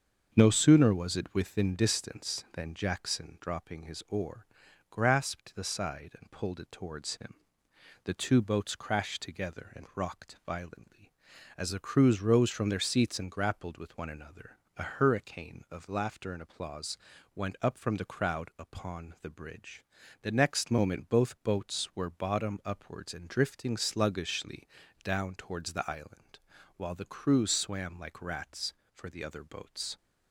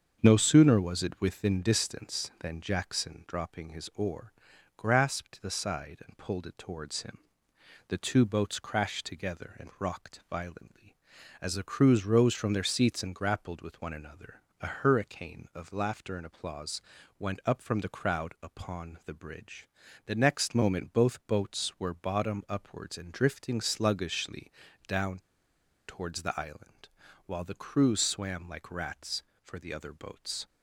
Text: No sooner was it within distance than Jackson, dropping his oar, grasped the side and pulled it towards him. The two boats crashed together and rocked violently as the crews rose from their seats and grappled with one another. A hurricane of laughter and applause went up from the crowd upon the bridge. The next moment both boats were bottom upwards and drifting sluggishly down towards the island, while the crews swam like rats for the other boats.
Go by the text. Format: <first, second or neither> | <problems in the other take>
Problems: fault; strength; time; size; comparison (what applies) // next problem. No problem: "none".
first | starts louder than the rest; until 1.2 s; 7 dB; also in the first // pauses between "applause" and "went"; at 16.8 s; 0.40 s long; also in the first // pauses between "sluggishly" and "down"; at 24.5 s; 0.38 s long; also in the first // pauses between "down" and "towards"; noticeable; at 25.1 s; 0.69 s long